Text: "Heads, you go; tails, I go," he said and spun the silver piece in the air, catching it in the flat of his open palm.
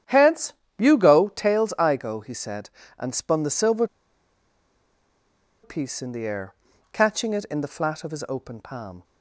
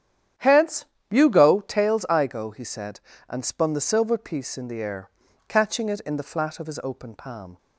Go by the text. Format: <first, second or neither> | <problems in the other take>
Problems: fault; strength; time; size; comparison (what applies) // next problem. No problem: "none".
second | starts louder than the rest; strong; until 1.3 s; 10 dB; strong in the second // pauses between "silver" and "piece"; strong; at 3.8 s; 1.7 s long